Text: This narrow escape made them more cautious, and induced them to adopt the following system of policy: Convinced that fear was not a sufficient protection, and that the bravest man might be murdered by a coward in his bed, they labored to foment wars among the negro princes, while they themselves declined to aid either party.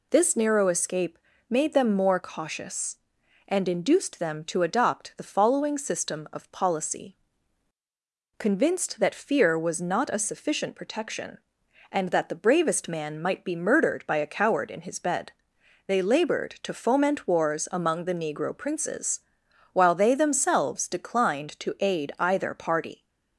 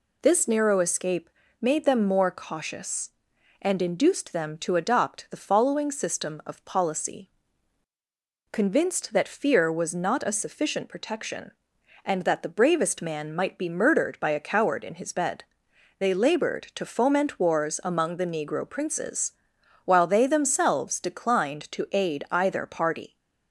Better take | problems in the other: neither | pauses between "escape" and "made"; slight; the same in both

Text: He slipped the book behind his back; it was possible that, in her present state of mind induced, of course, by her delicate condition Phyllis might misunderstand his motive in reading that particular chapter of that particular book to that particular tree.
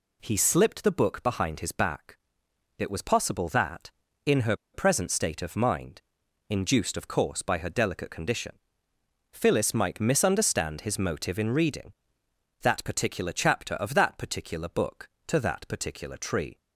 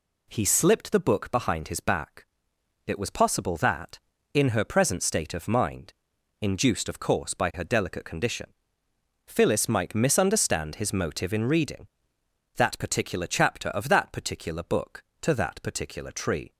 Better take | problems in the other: second | pauses between "her" and "present"; slight; at 4.5 s; 0.18 s long // pauses between "mind" and "induced"; noticeable; at 6.0 s; 0.48 s long; noticeable in the second // pauses between "condition" and "Phyllis"; noticeable; at 8.5 s; 0.80 s long; noticeable in the second

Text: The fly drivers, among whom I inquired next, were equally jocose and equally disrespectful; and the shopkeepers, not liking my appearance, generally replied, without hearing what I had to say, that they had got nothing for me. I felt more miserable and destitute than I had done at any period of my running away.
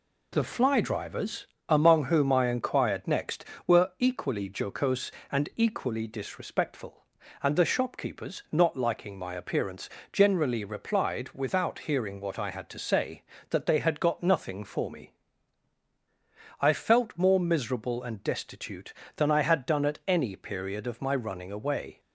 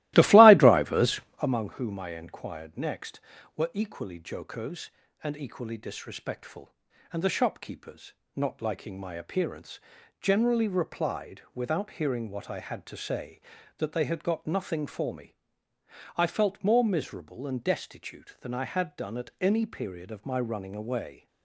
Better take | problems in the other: first | starts louder than the rest; strong; until 1.4 s; 17.5 dB

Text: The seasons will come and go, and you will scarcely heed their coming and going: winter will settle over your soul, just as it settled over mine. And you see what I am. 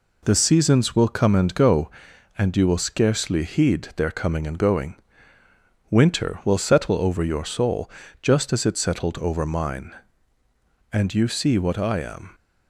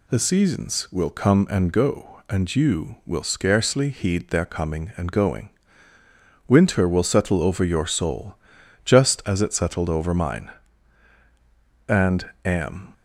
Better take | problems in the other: first | skips "you see what I"; at 12.3 s

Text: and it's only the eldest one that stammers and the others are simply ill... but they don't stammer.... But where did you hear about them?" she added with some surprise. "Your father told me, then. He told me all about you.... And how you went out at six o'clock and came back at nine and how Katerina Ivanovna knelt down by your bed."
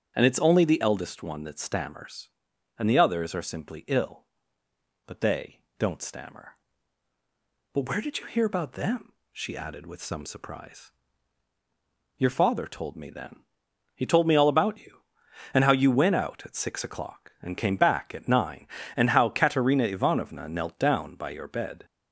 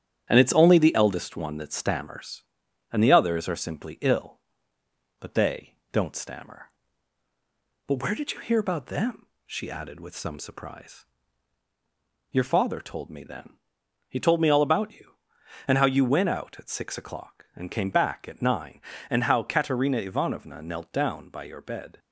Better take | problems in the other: first | gets quieter; throughout; 4 dB // starts louder than the rest; strong; until 1.3 s; 10 dB; strong in the first // pauses between "they" and "don't"; slight; at 5.7 s; 0.18 s long; slight in the first

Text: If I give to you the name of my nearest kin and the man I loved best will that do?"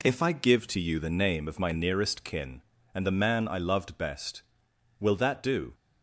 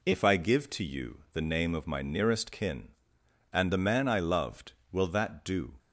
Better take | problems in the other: first | skips "best"; at 4.8 s

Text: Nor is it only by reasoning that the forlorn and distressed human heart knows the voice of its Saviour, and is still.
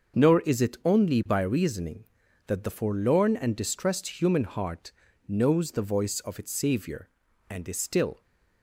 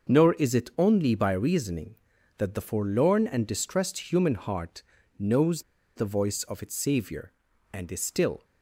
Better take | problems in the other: first | starts louder than the rest; until 1.1 s; 6.5 dB; also in the first // pauses between "heart" and "knows"; slight; at 4.8 s; 0.36 s long; slight in the first // pauses between "knows" and "the"; slight; at 5.6 s; 0.33 s long

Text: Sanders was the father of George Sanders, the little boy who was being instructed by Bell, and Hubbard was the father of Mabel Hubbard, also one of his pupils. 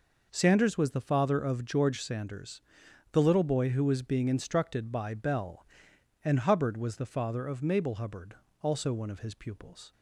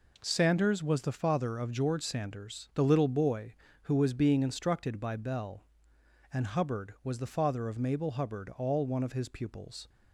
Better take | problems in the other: first | says "all" for "also"; at 8.5 s

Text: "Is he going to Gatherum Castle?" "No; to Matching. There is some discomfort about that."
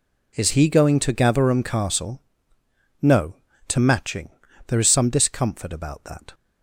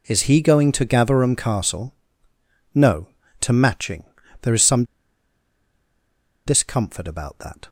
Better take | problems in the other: first | pauses between "some" and "discomfort"; strong; at 4.8 s; 1.6 s long

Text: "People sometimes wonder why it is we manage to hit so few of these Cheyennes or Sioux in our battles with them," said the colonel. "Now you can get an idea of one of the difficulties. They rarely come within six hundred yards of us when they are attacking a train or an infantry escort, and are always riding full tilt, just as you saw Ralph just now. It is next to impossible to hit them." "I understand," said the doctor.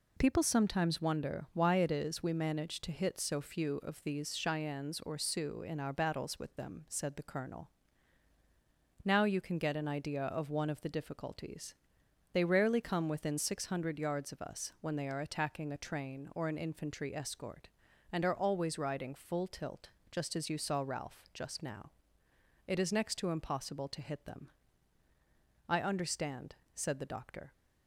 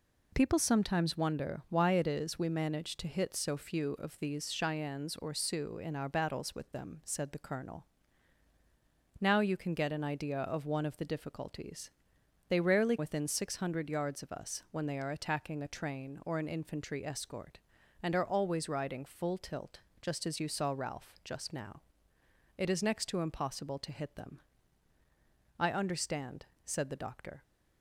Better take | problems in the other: first | skips "come"; at 12.9 s

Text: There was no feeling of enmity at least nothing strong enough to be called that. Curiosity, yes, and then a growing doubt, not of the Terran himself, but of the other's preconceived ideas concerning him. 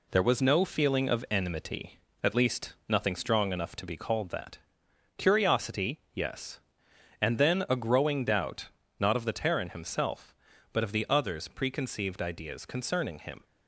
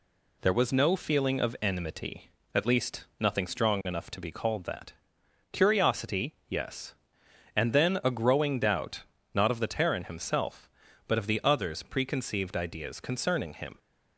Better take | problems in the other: second | gets quieter; noticeable; throughout; 5 dB

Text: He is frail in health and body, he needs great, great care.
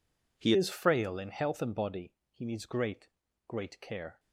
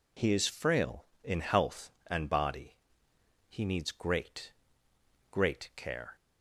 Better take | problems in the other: second | changes voice at "is"; from 0.5 s on; 3.6 s long

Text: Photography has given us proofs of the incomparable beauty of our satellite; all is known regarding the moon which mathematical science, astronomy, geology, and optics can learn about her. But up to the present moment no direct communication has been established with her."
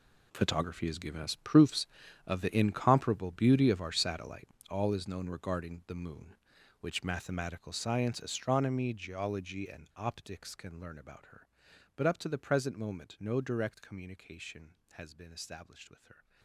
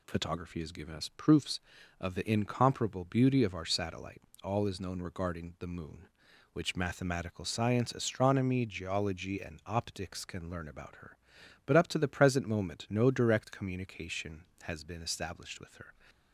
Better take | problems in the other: second | gets quieter; strong; throughout; 15.5 dB

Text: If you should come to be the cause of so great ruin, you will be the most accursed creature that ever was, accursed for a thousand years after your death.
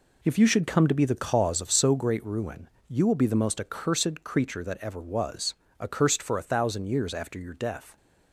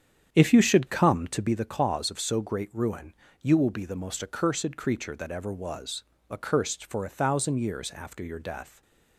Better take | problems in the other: first | starts louder than the rest; strong; until 1.5 s; 8.5 dB // stays silent after the last word; slight; from 8.6 s on; 0.5 s long

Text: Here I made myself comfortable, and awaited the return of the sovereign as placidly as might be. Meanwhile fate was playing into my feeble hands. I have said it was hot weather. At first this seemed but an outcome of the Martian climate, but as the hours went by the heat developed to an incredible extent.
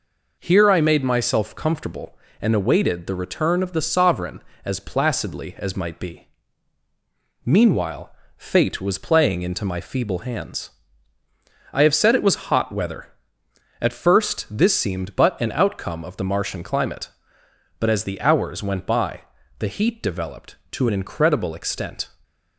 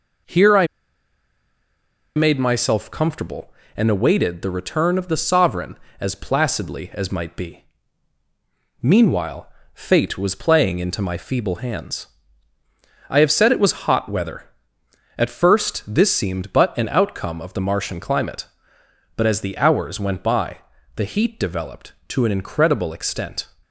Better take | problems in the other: first | pauses between "I" and "made"; strong; at 0.6 s; 1.4 s long // pauses between "Meanwhile" and "fate"; slight; at 9.4 s; 0.26 s long; slight in the first // pauses between "by" and "the"; slight; at 20.5 s; 0.36 s long; slight in the first

